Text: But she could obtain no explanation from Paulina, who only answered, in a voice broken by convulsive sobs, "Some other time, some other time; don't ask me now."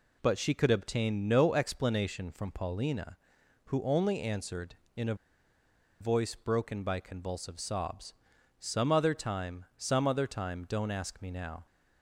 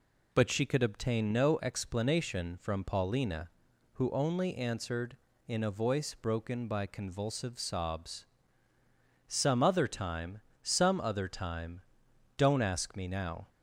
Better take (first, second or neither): second